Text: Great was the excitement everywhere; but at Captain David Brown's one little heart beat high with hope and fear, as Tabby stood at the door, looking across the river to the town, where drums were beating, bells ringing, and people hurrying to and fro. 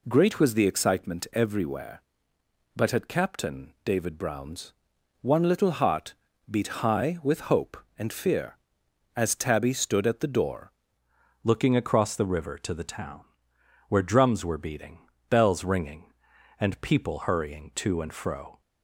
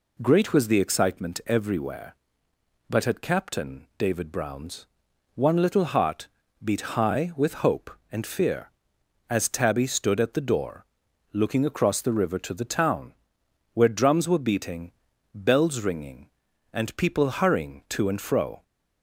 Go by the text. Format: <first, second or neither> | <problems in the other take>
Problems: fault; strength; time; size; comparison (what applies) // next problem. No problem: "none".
second | pauses between "Brown's" and "one"; noticeable; at 4.7 s; 0.48 s long; noticeable in the second // pauses between "heart" and "beat"; slight; at 6.1 s; 0.34 s long; slight in the second // changes voice at "looking"; from 11.4 s on; 7.1 s long